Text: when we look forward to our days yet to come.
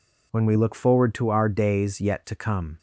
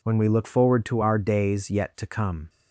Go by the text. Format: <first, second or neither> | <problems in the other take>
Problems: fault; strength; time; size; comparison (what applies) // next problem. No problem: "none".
neither | none